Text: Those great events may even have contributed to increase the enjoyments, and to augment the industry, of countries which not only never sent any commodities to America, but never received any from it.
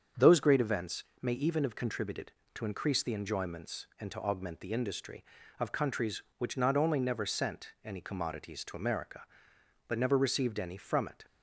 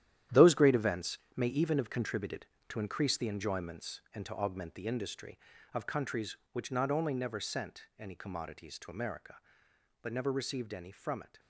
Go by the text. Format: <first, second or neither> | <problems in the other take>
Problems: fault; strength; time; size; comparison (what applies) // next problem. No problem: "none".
first | gets quieter; strong; throughout; 11 dB // starts louder than the rest; strong; until 1.5 s; 11 dB; strong in the first // pauses between "events" and "may"; slight; at 1.1 s; 0.18 s long; slight in the first